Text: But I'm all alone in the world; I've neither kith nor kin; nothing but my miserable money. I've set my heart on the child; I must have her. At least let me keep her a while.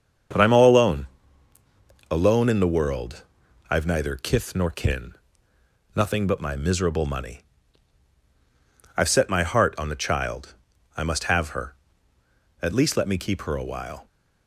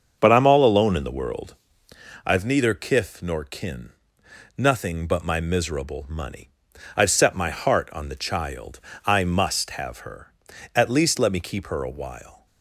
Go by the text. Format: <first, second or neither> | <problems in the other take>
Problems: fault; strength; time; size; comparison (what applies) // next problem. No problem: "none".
second | starts louder than the rest; strong; until 2.3 s; 7 dB; also in the second // says "alone" twice; at 2.0 s